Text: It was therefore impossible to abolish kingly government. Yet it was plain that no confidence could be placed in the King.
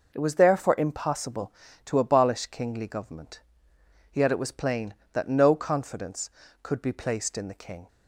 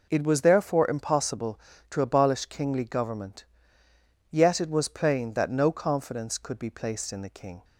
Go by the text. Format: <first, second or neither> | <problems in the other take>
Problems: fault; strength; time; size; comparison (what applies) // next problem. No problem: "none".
neither | none